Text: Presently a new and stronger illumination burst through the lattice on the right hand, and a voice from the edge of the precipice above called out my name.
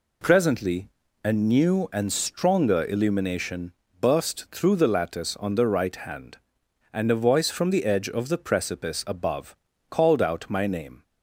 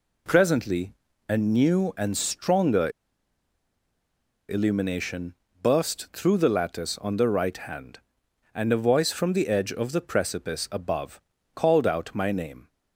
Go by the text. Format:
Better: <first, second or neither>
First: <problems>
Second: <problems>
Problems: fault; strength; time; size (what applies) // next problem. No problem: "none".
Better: first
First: pauses between "Presently" and "a"; slight; at 0.8 s; 0.36 s long // pauses between "illumination" and "burst"; slight; at 3.7 s; 0.28 s long // pauses between "above" and "called"; slight; at 9.5 s; 0.34 s long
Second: pauses between "Presently" and "a"; slight; at 0.9 s; 0.36 s long // pauses between "stronger" and "illumination"; strong; at 2.9 s; 1.5 s long // pauses between "illumination" and "burst"; slight; at 5.3 s; 0.28 s long // pauses between "above" and "called"; slight; at 11.1 s; 0.34 s long